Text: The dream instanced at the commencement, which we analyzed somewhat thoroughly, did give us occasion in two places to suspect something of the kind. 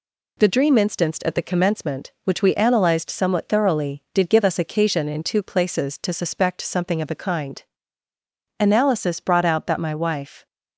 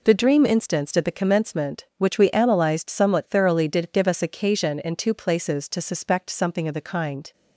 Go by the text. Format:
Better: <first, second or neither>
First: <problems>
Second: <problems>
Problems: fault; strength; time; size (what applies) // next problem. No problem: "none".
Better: second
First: goes on to say "Analysis brought out that my wife"; strong; from 8.6 s on; 1.8 s long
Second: none